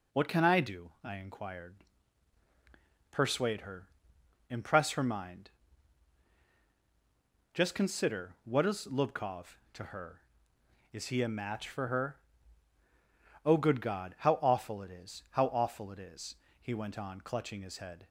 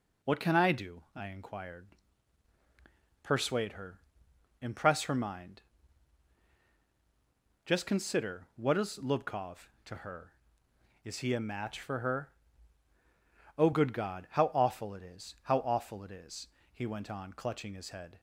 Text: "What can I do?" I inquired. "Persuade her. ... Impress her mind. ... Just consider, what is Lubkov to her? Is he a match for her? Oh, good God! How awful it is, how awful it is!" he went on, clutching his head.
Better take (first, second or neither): neither